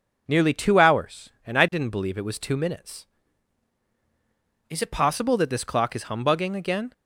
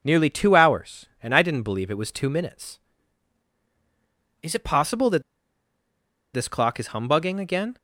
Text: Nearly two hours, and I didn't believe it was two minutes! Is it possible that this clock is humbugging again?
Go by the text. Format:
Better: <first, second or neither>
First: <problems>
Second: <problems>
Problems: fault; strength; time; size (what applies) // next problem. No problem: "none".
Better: first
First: none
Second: pauses between "that" and "this"; at 5.2 s; 1.1 s long